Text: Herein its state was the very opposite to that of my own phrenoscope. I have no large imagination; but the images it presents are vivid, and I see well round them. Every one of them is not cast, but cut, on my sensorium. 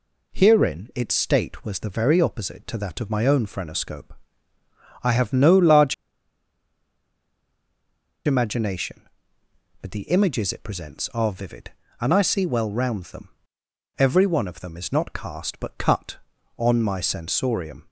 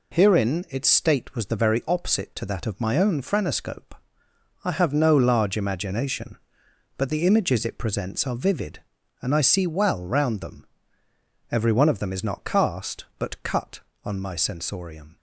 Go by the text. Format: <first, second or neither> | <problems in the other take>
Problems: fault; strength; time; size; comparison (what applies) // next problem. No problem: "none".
second | pauses between "large" and "imagination"; strong; at 5.9 s; 2.3 s long